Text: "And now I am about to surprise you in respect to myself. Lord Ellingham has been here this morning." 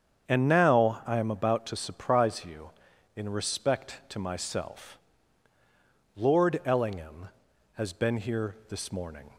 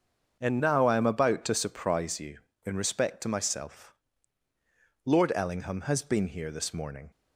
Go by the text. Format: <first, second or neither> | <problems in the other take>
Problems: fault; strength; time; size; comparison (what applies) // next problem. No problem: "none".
first | starts louder than the rest; until 1.4 s; 6.5 dB; strong in the first // changes voice at "now"; from 0.6 s on; 6.5 s long